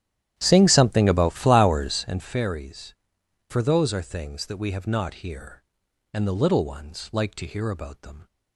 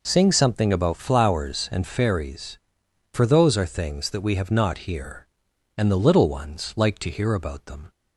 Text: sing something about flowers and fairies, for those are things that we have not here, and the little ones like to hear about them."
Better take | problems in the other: second | starts louder than the rest; strong; until 2.2 s; 11.5 dB

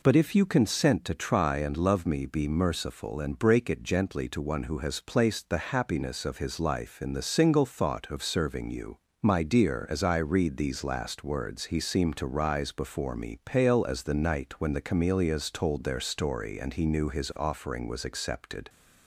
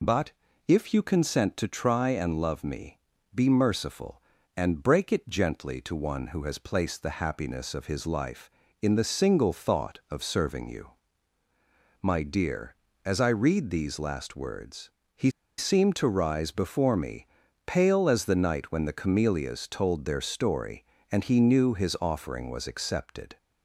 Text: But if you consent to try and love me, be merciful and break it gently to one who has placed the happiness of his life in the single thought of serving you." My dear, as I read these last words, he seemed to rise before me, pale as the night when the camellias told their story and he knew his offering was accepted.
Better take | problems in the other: first | pauses between "But" and "if"; slight; at 0.3 s; 0.34 s long // pauses between "he" and "seemed"; slight; at 15.3 s; 0.27 s long

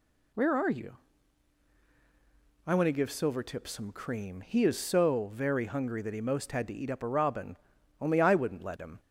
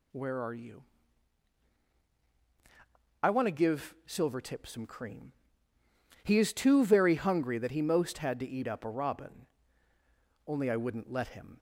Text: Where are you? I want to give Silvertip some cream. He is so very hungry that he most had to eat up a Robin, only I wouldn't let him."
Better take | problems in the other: first | says "too" for "so"; at 6.5 s

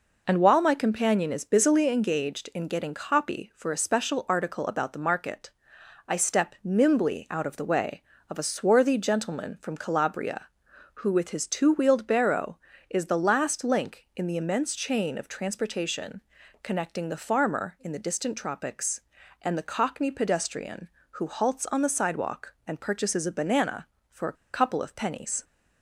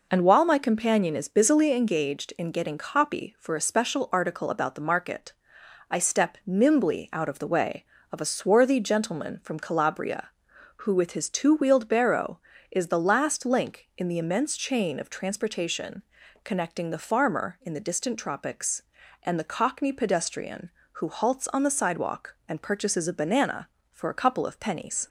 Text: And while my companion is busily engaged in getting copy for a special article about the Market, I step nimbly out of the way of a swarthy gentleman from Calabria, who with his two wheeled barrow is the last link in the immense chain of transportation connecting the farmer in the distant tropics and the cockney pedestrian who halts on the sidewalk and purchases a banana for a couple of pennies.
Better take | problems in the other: second | pauses between "transportation" and "connecting"; at 16.2 s; 0.42 s long; also in the second // pauses between "a" and "couple"; slight; at 24.3 s; 0.19 s long

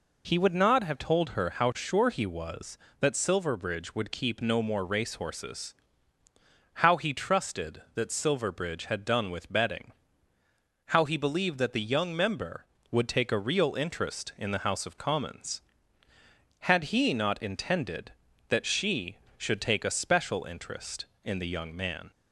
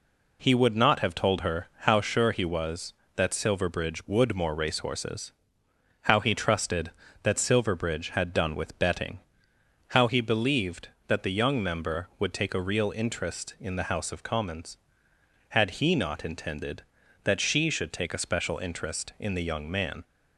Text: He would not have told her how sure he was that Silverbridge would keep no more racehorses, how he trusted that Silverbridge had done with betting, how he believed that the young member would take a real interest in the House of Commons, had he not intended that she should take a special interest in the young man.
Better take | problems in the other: first | skips "keep no"; at 4.3 s

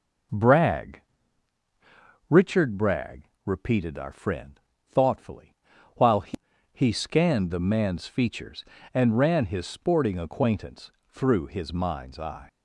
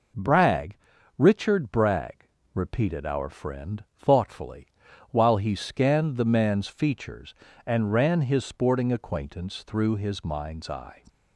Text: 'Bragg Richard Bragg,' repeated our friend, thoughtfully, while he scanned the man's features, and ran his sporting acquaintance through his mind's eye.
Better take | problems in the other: second | pauses between "Bragg" and "Richard"; strong; at 1.0 s; 1.2 s long; also in the second // says "he" twice; at 6.7 s // pauses between "acquaintance" and "through"; slight; at 10.9 s; 0.18 s long

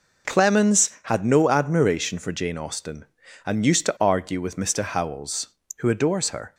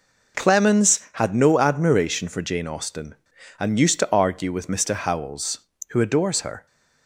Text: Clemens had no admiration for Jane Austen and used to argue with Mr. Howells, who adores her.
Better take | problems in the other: neither | none

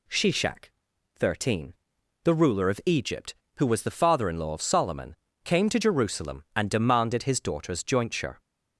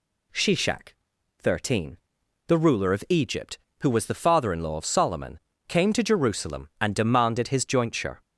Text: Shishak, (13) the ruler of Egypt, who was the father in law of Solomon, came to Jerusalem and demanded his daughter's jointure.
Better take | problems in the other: first | skips "daughter's"; at 7.6 s

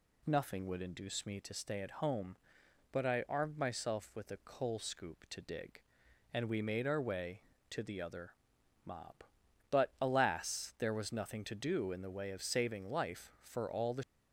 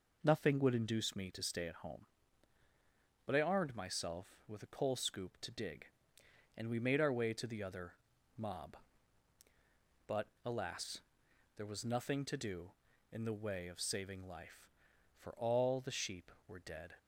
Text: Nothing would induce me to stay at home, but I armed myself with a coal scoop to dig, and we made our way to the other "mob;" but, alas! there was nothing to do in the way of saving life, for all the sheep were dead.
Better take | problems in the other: second | pauses between "other" and "mob"; noticeable; at 8.3 s; 0.54 s long; also in the second // stops before "sheep were dead"; at 14.0 s

